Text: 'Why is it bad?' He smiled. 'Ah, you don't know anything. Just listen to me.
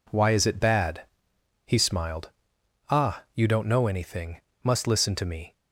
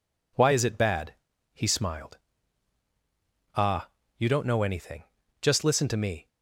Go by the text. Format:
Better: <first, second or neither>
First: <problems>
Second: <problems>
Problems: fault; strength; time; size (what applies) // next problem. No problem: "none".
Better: second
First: says "Must" for "Just"; at 4.6 s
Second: none